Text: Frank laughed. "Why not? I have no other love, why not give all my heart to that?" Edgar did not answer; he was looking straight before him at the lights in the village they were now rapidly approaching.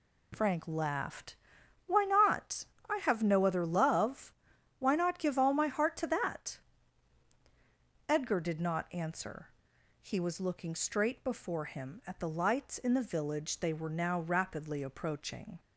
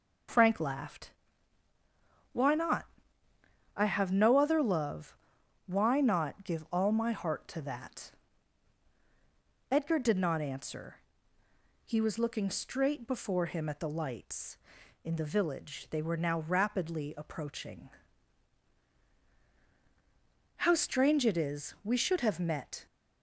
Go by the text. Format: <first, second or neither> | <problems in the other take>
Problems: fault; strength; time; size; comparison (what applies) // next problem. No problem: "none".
first | goes on to say "How strange it is we should have met"; strong; from 20.5 s on; 2.2 s long